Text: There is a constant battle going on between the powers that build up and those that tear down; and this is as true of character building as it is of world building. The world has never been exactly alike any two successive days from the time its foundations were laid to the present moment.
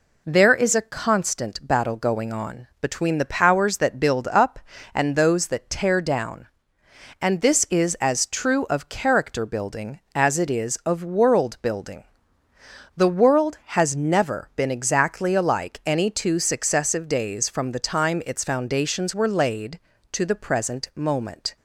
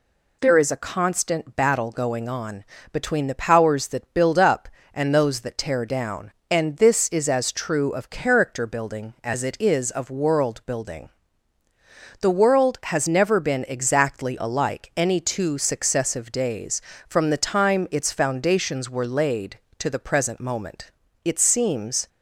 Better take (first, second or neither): first